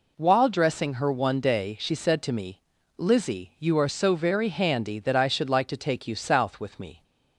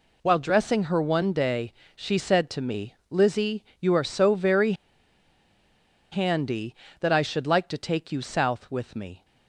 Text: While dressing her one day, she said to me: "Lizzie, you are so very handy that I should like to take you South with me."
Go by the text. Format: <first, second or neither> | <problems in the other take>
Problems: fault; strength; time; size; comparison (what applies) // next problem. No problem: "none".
first | pauses between "very" and "handy"; strong; at 4.7 s; 1.3 s long